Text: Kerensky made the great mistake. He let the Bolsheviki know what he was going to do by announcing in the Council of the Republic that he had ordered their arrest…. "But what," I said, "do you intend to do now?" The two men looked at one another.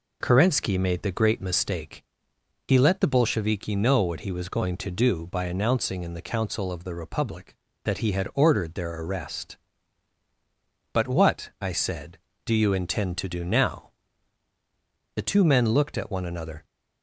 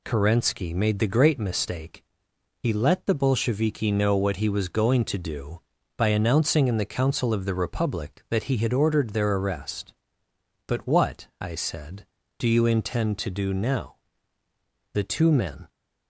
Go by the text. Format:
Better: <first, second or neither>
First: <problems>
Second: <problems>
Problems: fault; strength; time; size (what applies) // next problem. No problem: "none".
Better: first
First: none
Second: stops before "looked at one another"; at 15.6 s